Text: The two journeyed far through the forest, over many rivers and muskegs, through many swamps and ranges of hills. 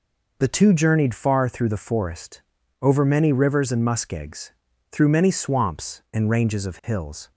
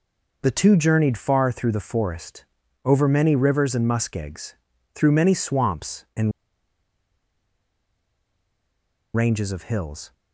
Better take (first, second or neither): first